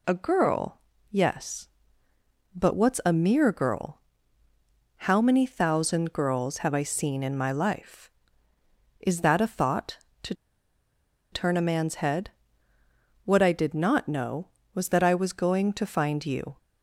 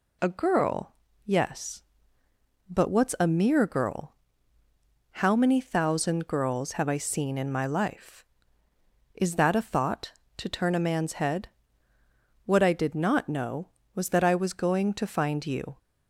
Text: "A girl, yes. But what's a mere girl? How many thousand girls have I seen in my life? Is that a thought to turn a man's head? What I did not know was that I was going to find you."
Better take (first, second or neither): second